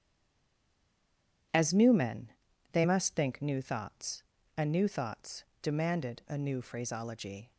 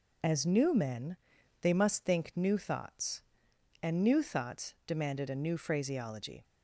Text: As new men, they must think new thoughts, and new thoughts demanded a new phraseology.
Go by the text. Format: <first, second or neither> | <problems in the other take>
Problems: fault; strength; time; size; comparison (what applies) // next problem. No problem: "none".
second | stays silent before the first word; noticeable; until 1.5 s; 1.5 s long // starts louder than the rest; strong; until 2.9 s; 9.5 dB // pauses between "thoughts" and "demanded"; slight; at 5.4 s; 0.16 s long